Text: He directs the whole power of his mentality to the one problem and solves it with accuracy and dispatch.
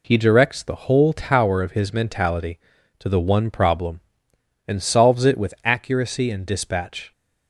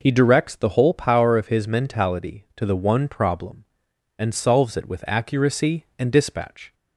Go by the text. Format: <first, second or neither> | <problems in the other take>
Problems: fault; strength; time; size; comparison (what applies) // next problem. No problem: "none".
second | says "tower" for "power"; at 1.1 s